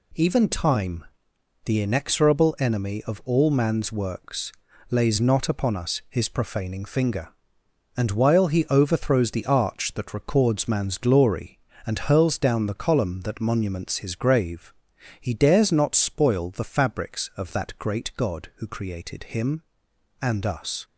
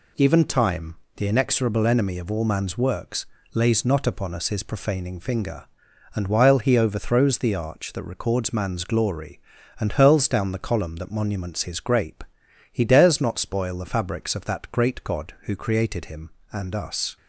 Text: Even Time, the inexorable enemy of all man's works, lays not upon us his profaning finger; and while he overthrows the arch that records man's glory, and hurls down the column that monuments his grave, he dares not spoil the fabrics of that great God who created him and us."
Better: first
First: none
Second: says "grape" for "grave"; at 11.7 s

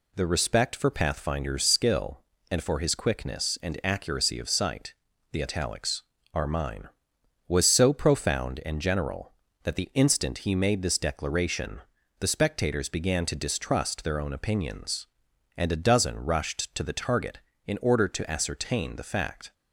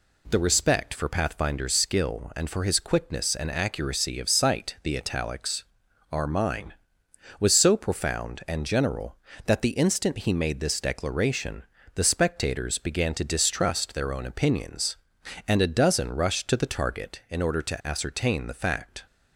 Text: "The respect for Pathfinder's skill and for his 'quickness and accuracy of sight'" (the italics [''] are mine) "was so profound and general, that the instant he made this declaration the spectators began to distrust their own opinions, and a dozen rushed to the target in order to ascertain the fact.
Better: neither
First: pauses between "declaration" and "the"; at 11.7 s; 0.40 s long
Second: pauses between "declaration" and "the"; slight; at 11.6 s; 0.32 s long

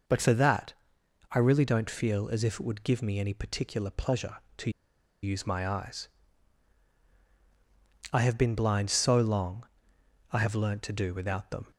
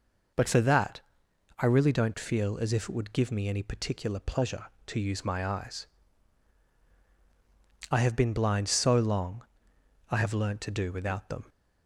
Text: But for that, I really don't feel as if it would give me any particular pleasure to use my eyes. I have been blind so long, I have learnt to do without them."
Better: second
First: pauses between "to" and "use"; noticeable; at 4.6 s; 0.53 s long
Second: none

